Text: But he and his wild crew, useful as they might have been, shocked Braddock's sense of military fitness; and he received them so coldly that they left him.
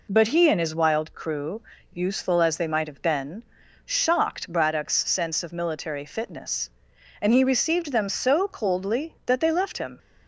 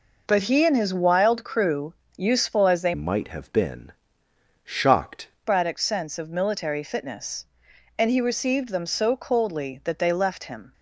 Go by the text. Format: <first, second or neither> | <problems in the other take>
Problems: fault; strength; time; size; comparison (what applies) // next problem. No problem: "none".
first | changes voice from "might" to "shocked"; from 2.9 to 5.2 s; 2.3 s long